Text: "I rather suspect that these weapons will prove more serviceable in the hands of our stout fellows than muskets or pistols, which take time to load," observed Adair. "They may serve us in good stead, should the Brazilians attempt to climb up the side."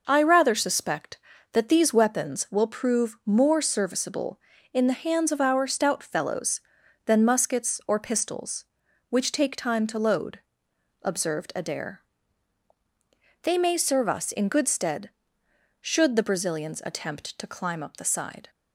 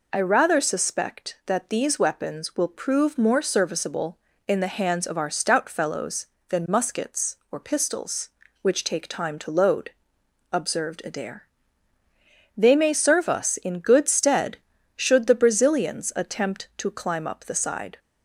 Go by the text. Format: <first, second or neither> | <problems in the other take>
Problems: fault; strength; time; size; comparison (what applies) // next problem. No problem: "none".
neither | none